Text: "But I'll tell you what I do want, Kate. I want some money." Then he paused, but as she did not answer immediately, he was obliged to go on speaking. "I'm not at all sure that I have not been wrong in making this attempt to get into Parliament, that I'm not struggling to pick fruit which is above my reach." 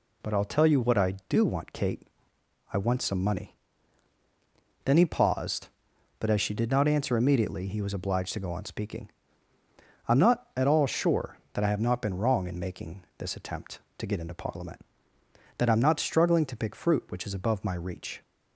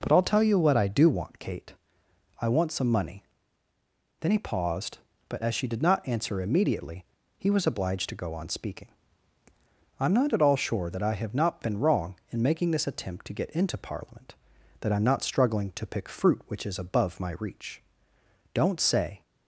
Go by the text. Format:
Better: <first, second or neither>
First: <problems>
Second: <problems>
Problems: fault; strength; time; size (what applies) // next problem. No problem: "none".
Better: first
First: none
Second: goes on to say "Don't say"; noticeable; from 18.5 s on; 0.68 s long